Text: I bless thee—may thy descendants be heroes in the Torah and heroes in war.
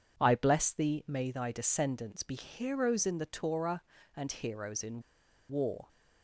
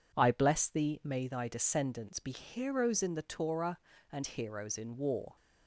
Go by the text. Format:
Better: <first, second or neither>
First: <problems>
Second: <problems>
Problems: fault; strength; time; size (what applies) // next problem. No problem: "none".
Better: second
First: pauses between "in" and "war"; noticeable; at 5.0 s; 0.47 s long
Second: none